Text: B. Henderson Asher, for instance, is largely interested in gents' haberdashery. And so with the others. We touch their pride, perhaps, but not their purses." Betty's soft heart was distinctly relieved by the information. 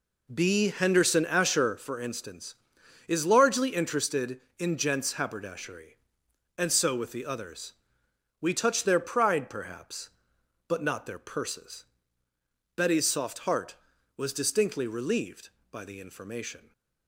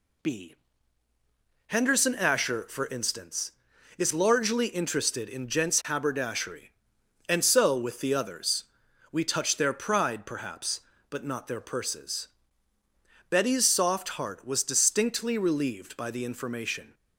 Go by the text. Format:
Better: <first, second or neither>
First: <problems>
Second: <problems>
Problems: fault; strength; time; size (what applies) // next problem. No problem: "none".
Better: second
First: starts louder than the rest; noticeable; until 1.8 s; 4 dB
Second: none